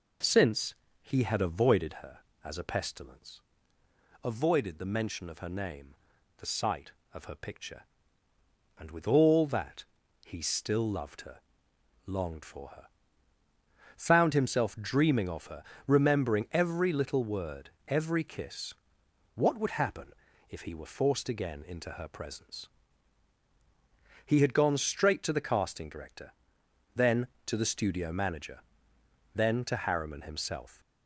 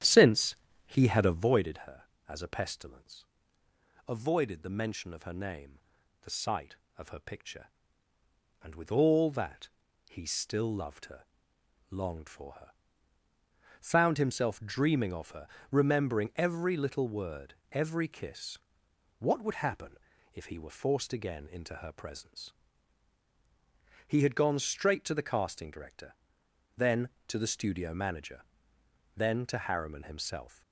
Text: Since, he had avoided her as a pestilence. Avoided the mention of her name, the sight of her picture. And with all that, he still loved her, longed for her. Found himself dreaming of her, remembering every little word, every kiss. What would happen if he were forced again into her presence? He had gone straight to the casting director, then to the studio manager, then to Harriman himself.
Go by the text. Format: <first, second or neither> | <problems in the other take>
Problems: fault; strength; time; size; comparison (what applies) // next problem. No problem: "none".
first | starts louder than the rest; strong; until 1.5 s; 10.5 dB // pauses between "happen" and "if"; slight; at 19.9 s; 0.36 s long; slight in the first